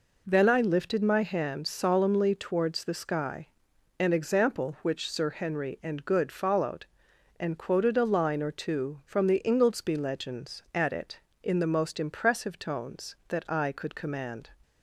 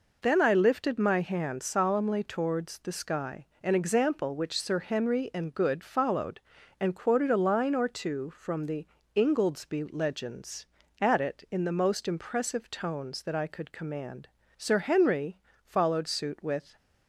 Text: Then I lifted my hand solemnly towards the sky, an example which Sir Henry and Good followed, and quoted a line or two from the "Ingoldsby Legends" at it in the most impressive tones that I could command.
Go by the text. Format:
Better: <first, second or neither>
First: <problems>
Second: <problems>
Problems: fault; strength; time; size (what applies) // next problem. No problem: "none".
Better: first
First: none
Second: pauses between "the" and "Ingoldsby"; slight; at 8.8 s; 0.28 s long // goes on to say "Sir Henry followed suit with"; strong; from 14.5 s on; 2.2 s long